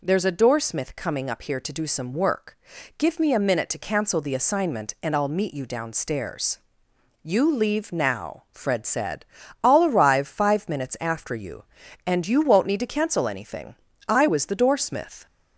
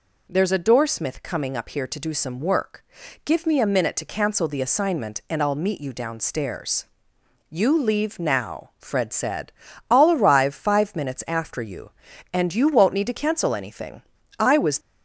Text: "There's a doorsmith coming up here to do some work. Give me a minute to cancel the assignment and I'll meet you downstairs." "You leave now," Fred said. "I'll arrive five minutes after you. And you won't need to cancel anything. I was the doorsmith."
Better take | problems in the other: first | stops before "the doorsmith"; at 14.7 s

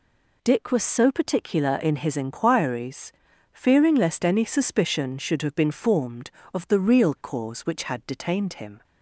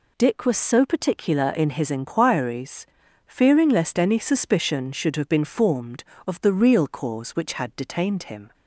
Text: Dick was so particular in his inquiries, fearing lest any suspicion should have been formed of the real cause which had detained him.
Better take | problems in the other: neither | none

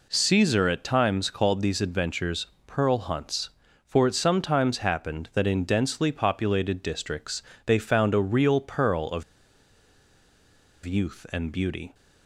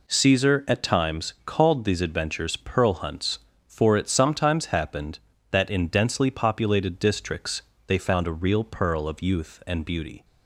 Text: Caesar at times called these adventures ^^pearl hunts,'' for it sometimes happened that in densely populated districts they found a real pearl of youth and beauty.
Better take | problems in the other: second | pauses between "adventures" and "pearl"; slight; at 2.4 s; 0.20 s long // pauses between "districts" and "they"; slight; at 7.4 s; 0.24 s long; slight in the second // pauses between "of" and "youth"; strong; at 9.2 s; 1.6 s long

